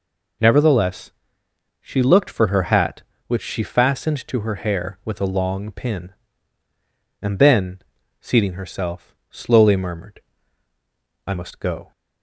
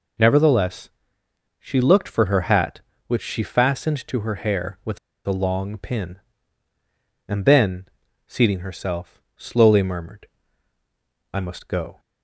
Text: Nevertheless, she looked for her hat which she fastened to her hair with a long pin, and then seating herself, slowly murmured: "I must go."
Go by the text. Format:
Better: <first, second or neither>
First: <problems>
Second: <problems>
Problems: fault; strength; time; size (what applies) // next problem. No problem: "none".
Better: first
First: pauses between "then" and "seating"; at 7.7 s; 0.40 s long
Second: pauses between "with" and "a"; slight; at 4.9 s; 0.29 s long // pauses between "then" and "seating"; at 7.8 s; 0.40 s long